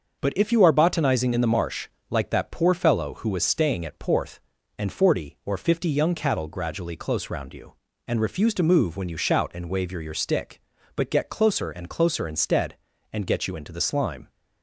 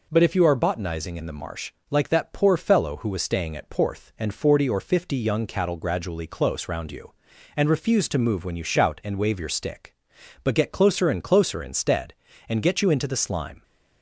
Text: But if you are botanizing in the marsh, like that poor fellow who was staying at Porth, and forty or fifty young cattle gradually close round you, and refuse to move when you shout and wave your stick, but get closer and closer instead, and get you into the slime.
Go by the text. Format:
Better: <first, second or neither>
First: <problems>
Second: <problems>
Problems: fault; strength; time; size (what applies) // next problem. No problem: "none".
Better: second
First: starts louder than the rest; until 1.2 s; 6.5 dB // says "your" twice; at 10.0 s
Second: none